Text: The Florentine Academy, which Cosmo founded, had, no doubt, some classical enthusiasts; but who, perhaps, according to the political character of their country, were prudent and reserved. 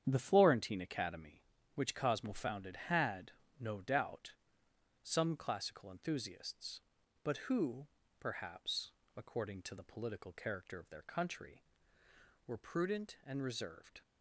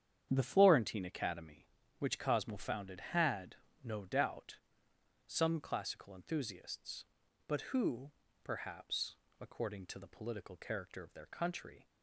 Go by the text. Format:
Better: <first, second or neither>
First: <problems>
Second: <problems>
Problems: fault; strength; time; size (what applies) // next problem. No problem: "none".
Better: first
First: starts louder than the rest; strong; until 1.0 s; 9 dB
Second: starts louder than the rest; strong; until 1.3 s; 9 dB // stops before "were prudent and reserved"; at 11.8 s